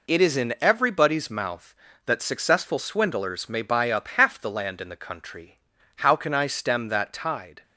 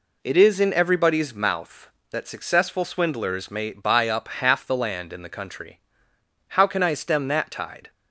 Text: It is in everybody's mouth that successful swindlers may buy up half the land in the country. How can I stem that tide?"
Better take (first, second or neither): neither